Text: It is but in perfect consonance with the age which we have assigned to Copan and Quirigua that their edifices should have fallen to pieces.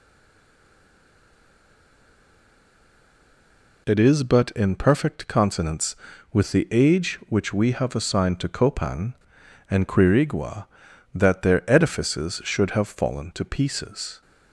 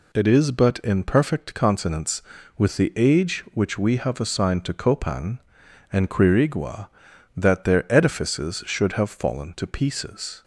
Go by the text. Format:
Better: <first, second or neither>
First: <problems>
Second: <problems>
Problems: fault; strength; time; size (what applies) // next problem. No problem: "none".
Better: second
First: stays silent before the first word; strong; until 3.8 s; 3.8 s long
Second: none